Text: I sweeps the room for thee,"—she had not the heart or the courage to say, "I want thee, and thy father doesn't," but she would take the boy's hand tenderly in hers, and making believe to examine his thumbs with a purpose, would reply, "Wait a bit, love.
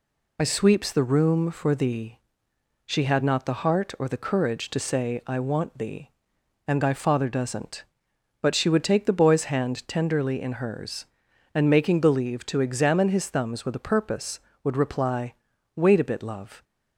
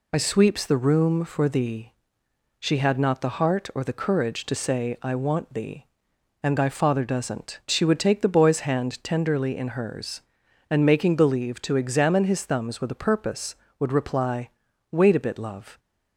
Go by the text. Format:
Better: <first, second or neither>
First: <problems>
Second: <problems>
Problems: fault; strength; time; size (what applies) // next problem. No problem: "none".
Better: first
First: none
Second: skips "but"; at 7.6 s